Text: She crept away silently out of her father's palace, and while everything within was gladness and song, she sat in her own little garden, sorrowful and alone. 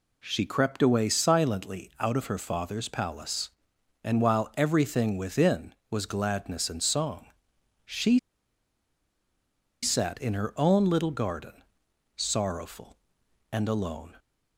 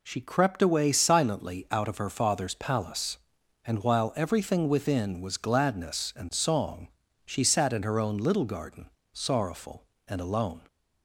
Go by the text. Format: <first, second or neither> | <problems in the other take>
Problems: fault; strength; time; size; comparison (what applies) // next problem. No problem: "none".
second | pauses between "she" and "sat"; strong; at 8.1 s; 1.6 s long